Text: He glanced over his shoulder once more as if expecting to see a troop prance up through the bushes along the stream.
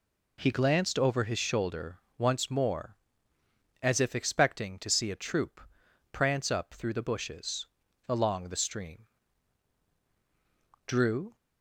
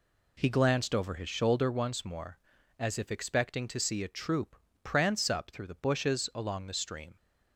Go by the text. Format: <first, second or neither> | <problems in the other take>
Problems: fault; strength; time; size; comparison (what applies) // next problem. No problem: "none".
second | pauses between "shoulder" and "once"; slight; at 1.9 s; 0.18 s long // pauses between "troop" and "prance"; noticeable; at 5.5 s; 0.54 s long; slight in the second // pauses between "bushes" and "along"; at 7.6 s; 0.40 s long // goes on to say "Drew"; slight; from 10.8 s on; 0.48 s long